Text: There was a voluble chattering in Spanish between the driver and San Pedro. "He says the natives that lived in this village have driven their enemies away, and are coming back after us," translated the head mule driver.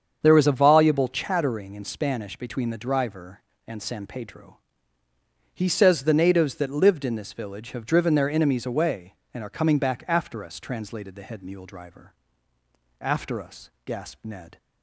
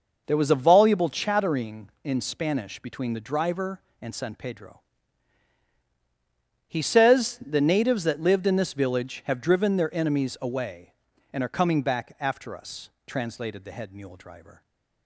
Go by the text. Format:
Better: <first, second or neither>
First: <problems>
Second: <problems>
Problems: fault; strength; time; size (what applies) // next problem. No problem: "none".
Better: second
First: starts louder than the rest; strong; until 1.2 s; 7.5 dB // goes on to say "After us gasped Ned"; from 12.9 s on; 1.5 s long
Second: none